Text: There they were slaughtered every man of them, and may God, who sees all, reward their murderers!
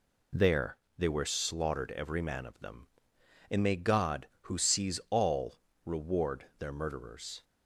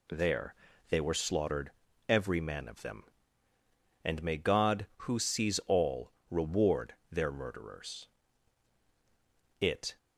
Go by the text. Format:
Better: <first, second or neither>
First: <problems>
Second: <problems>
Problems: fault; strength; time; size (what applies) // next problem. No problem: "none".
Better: first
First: pauses between "There" and "they"; slight; at 0.7 s; 0.20 s long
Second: pauses between "There" and "they"; slight; at 0.5 s; 0.32 s long // pauses between "slaughtered" and "every"; slight; at 1.7 s; 0.36 s long // pauses between "reward" and "their"; slight; at 6.9 s; 0.18 s long // goes on to say "It"; slight; from 9.5 s on; 0.38 s long